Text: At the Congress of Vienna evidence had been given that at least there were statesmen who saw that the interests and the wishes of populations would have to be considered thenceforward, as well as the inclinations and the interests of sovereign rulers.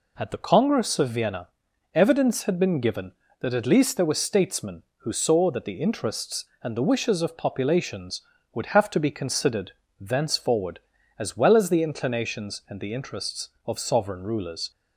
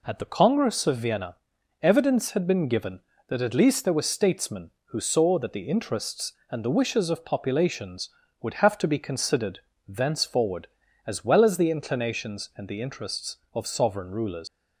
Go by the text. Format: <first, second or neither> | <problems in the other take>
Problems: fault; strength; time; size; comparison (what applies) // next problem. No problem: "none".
first | pauses between "Vienna" and "evidence"; noticeable; at 1.3 s; 0.46 s long; noticeable in the first // pauses between "considered" and "thenceforward"; slight; at 9.6 s; 0.28 s long; slight in the first // leaves "rulers" unfinished; at 14.4 s; 105 ms